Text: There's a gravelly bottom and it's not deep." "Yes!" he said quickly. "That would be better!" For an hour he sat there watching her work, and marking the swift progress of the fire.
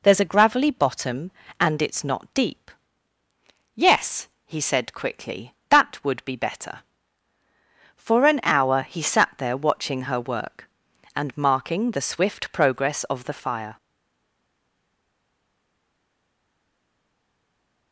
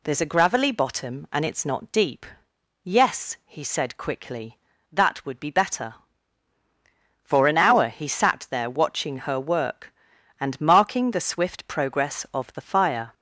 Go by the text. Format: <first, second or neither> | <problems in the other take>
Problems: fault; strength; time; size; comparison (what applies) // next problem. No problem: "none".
second | stays silent after the last word; strong; from 13.7 s on; 4.2 s long